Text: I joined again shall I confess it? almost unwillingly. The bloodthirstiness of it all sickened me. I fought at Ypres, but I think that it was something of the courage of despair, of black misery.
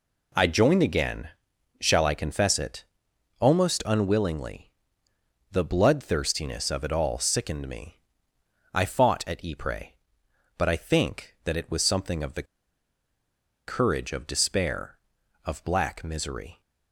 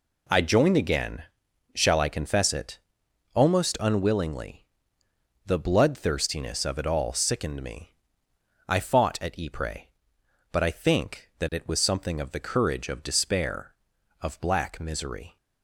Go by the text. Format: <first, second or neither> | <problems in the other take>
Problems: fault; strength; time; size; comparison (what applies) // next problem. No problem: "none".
second | pauses between "again" and "shall"; noticeable; at 1.2 s; 0.50 s long; noticeable in the second // pauses between "the" and "courage"; at 12.4 s; 1.2 s long